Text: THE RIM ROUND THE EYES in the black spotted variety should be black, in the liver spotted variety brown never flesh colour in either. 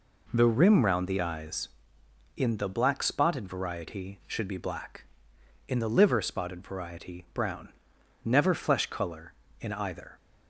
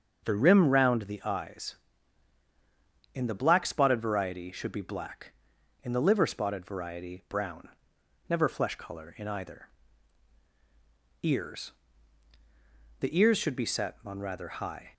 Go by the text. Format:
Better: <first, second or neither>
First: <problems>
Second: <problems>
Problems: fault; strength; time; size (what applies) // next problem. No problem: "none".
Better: first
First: pauses between "brown" and "never"; noticeable; at 7.6 s; 0.56 s long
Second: starts louder than the rest; until 1.2 s; 6.5 dB // pauses between "brown" and "never"; noticeable; at 7.6 s; 0.62 s long // goes on to say "EARS The ears should be set on rather high"; strong; from 11.2 s on; 3.7 s long